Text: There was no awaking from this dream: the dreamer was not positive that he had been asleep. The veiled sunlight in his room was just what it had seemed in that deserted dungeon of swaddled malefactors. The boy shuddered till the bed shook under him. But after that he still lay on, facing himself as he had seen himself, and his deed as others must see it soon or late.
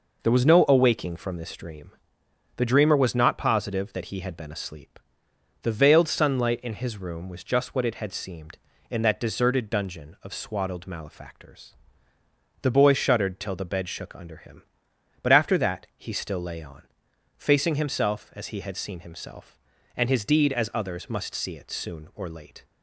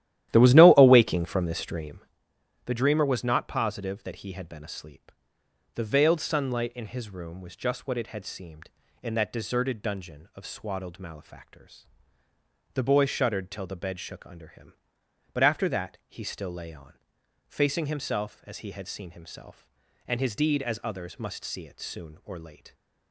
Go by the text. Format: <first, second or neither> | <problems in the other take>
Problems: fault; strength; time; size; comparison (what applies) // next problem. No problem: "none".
first | starts louder than the rest; strong; until 2.1 s; 13 dB